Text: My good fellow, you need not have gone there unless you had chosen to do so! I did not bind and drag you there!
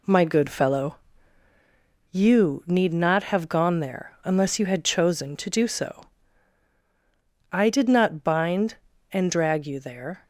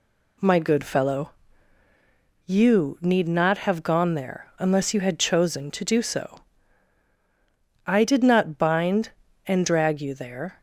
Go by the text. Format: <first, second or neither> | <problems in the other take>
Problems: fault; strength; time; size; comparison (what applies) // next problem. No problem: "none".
second | gets quieter; noticeable; throughout; 6 dB